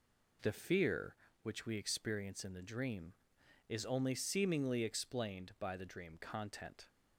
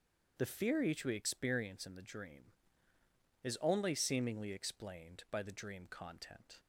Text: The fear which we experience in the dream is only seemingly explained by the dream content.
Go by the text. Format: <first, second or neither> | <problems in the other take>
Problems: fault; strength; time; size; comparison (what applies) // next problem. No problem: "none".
first | starts louder than the rest; strong; until 1.3 s; 7.5 dB // says "each" for "which"; at 0.8 s